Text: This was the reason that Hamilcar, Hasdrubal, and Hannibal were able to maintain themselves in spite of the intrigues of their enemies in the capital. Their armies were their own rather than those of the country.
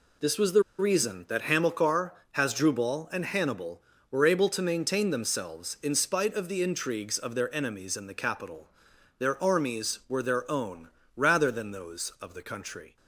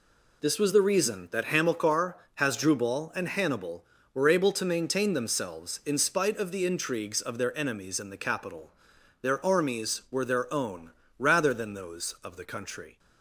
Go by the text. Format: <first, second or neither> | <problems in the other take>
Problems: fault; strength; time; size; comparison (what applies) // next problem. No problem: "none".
second | pauses between "the" and "reason"; slight; at 0.6 s; 0.16 s long // pauses between "own" and "rather"; slight; at 10.8 s; 0.28 s long; slight in the second